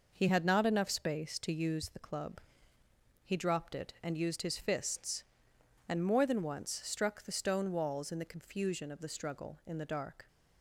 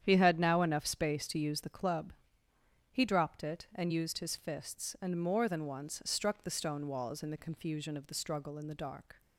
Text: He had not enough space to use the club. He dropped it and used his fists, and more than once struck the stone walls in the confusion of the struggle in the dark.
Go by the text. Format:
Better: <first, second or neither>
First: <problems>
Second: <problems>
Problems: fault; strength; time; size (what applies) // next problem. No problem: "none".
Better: first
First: none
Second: starts louder than the rest; strong; until 1.0 s; 9.5 dB // says "now" for "not"; at 0.3 s